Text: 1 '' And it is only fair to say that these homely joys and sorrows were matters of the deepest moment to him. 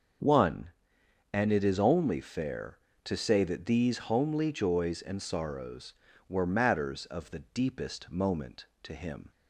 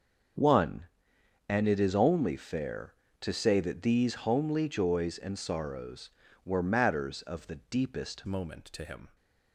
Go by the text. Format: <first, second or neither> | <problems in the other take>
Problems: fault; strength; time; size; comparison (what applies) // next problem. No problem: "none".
first | changes voice at "moment"; from 8.2 s on; 0.9 s long